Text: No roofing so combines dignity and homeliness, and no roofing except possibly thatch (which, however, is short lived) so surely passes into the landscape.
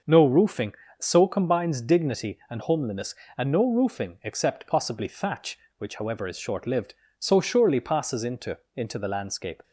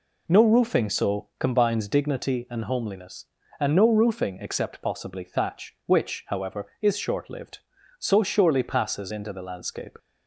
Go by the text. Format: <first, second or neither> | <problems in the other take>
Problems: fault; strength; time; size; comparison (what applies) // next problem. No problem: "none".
second | starts louder than the rest; until 1.2 s; 6.5 dB // says "into" twice; at 8.7 s